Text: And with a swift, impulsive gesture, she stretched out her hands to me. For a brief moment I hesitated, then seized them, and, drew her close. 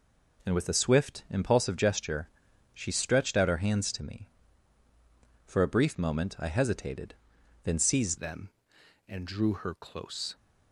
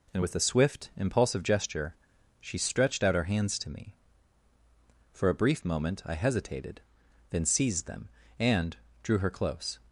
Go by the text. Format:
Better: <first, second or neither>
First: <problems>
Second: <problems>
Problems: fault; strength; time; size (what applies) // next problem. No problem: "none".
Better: second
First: changes voice at "them"; from 8.1 s on; 2.2 s long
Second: none